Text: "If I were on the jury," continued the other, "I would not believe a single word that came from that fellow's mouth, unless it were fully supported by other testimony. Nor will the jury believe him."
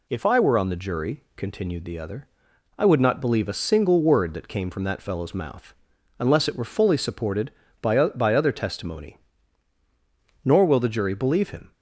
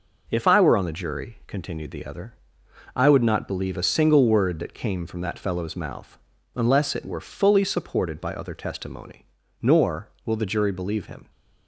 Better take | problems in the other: second | says "by" twice; at 8.0 s

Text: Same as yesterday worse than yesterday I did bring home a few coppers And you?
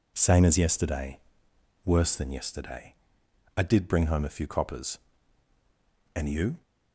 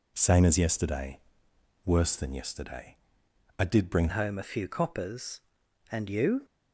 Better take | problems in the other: first | pauses between "yesterday" and "worse"; noticeable; at 1.1 s; 0.66 s long; noticeable in the first // pauses between "yesterday" and "I"; noticeable; at 2.9 s; 0.62 s long; noticeable in the first // changes voice at "home"; from 4.0 s on; 2.4 s long

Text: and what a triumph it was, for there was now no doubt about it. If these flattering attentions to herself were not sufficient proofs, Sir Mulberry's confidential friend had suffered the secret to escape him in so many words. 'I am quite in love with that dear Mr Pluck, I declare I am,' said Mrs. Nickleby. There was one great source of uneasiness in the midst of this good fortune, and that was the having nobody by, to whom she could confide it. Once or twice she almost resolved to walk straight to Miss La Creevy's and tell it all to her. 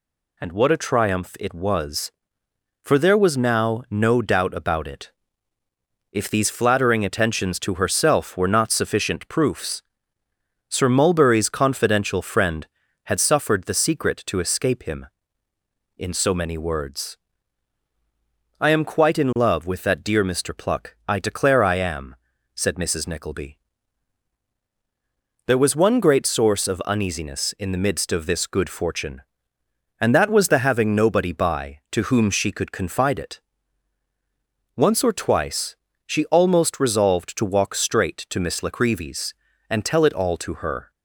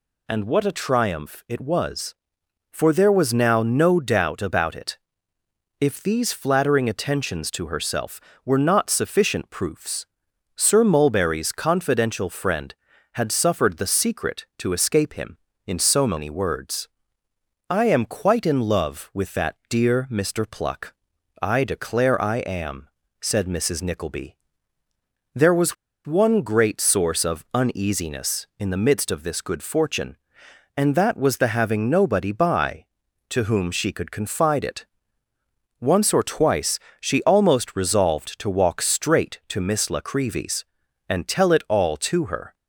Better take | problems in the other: first | pauses between "was" and "one"; slight; at 25.7 s; 0.30 s long // pauses between "twice" and "she"; slight; at 36.8 s; 0.20 s long; slight in the first

